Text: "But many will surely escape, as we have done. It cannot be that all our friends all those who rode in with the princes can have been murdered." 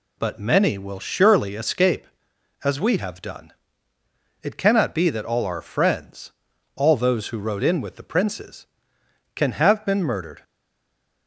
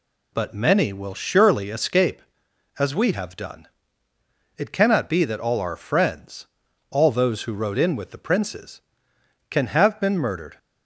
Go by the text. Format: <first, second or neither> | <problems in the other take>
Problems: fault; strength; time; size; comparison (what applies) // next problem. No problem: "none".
second | pauses between "friends" and "all"; at 6.3 s; 0.42 s long; also in the second // stays silent after the last word; slight; from 10.4 s on; 0.8 s long